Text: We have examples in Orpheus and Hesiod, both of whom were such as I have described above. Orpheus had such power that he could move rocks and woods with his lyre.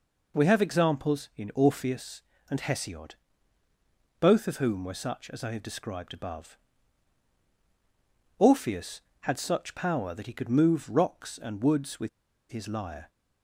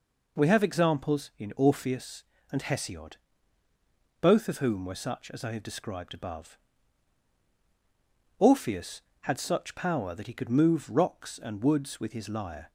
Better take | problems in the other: second | pauses between "with" and "his"; at 12.0 s; 0.41 s long

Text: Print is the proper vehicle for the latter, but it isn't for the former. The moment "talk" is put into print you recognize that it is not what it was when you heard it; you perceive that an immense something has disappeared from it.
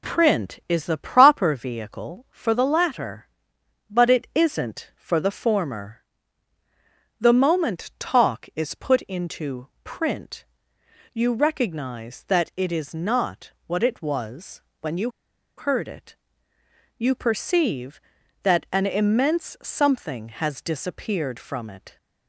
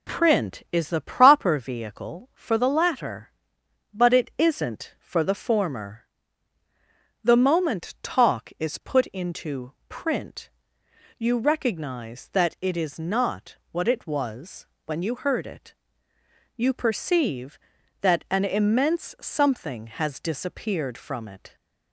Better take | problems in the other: second | pauses between "print" and "you"; noticeable; at 10.4 s; 0.70 s long; noticeable in the second // pauses between "was" and "when"; slight; at 14.6 s; 0.22 s long; slight in the second // pauses between "you" and "heard"; noticeable; at 15.0 s; 0.49 s long

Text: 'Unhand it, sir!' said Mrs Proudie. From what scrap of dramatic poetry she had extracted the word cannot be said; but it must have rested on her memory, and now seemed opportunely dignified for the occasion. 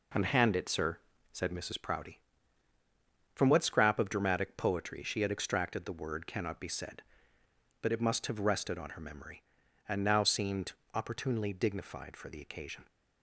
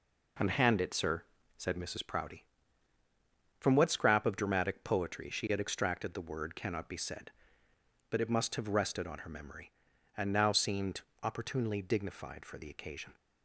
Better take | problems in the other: neither | pauses between "seemed" and "opportunely"; slight; the same in both

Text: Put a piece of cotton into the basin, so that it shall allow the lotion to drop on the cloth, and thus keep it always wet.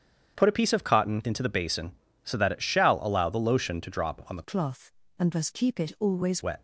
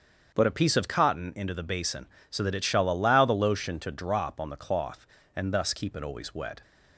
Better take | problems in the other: second | starts louder than the rest; strong; until 1.3 s; 8 dB; strong in the second // changes voice from "cloth" to "always"; from 4.4 to 6.4 s; 2.0 s long

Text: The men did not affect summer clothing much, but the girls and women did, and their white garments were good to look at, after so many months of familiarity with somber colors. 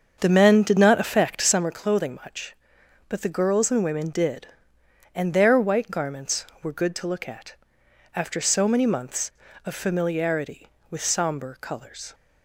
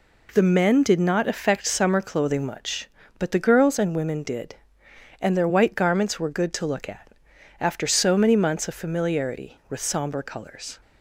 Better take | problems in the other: second | starts louder than the rest; until 1.7 s; 7 dB

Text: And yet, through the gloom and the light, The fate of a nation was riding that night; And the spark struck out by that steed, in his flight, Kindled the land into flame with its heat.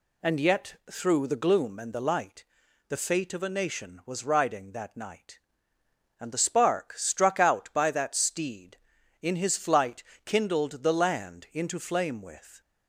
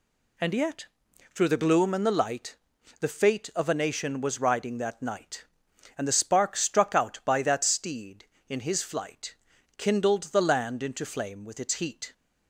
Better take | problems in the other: second | stops before "its heat"; at 12.6 s

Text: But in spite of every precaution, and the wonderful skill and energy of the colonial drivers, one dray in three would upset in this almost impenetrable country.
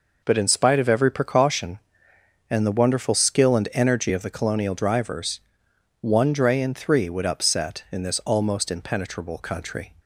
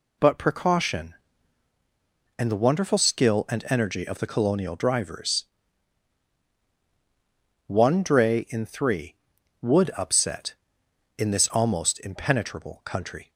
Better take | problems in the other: first | skips "in spite of every"; at 0.3 s

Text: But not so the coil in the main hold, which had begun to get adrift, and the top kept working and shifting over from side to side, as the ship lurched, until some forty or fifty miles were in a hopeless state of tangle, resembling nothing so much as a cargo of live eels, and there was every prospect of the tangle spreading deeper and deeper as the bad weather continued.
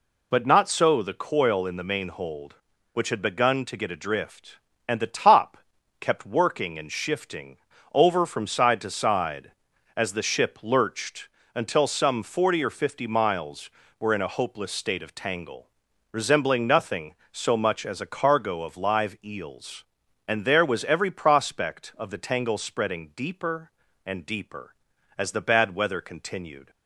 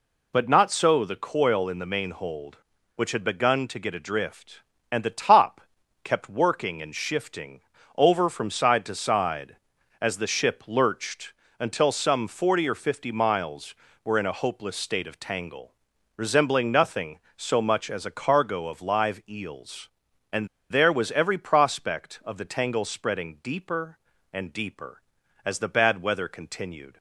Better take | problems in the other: first | pauses between "top" and "kept"; at 5.6 s; 0.42 s long; also in the first // pauses between "shifting" and "over"; slight; at 7.6 s; 0.36 s long; slight in the first // pauses between "and" and "there"; slight; at 20.4 s; 0.25 s long

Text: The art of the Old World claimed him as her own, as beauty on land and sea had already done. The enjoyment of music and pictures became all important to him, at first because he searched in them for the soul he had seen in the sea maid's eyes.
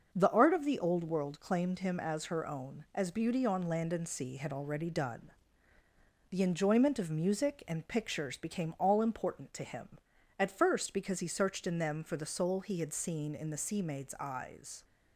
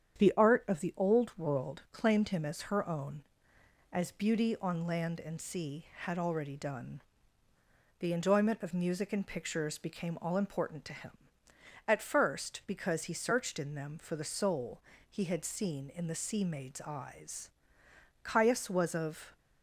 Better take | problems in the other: first | starts louder than the rest; strong; until 1.2 s; 8.5 dB; also in the first // pauses between "soul" and "he"; slight; at 14.8 s; 0.26 s long // goes on to say "Caius was of"; noticeable; from 18.2 s on; 1.1 s long

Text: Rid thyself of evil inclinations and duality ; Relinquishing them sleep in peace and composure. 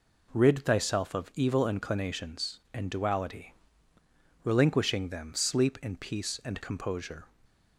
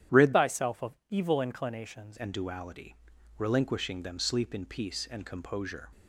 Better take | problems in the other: first | starts louder than the rest; strong; until 1.2 s; 10.5 dB // changes voice from "thyself" to "inclinations"; from 0.3 to 2.1 s; 1.8 s long

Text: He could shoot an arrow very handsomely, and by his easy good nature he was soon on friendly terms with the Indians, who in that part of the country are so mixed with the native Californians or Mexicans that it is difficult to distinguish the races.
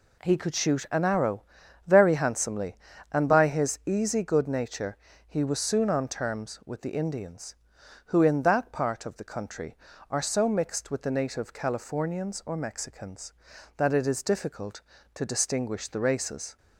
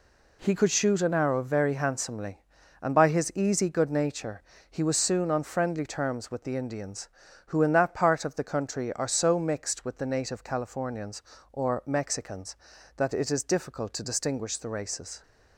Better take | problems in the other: second | pauses between "arrow" and "very"; at 1.4 s; 0.44 s long // pauses between "nature" and "he"; slight; at 4.9 s; 0.30 s long; slight in the second // skips "friendly"; at 6.0 s

